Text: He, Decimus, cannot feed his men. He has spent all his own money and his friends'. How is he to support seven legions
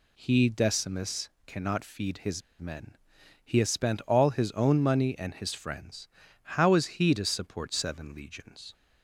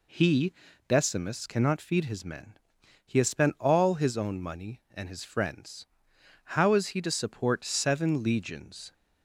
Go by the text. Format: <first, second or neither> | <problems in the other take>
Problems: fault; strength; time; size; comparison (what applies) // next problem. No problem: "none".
second | pauses between "his" and "men"; slight; at 2.4 s; 0.17 s long